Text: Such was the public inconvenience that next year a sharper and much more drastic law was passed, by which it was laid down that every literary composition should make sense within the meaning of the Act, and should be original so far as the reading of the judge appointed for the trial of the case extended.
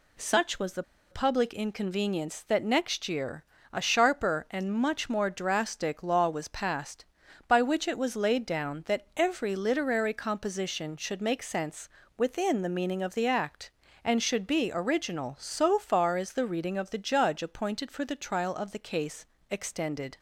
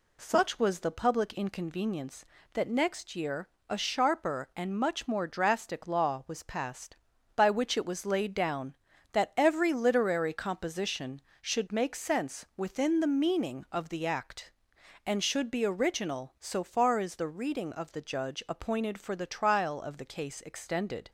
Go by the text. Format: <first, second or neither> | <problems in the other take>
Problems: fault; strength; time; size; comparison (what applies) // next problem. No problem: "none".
second | pauses between "the" and "public"; slight; at 0.8 s; 0.29 s long // pauses between "year" and "a"; slight; at 3.4 s; 0.28 s long; slight in the second // pauses between "sense" and "within"; slight; at 11.8 s; 0.30 s long // pauses between "case" and "extended"; slight; at 19.2 s; 0.24 s long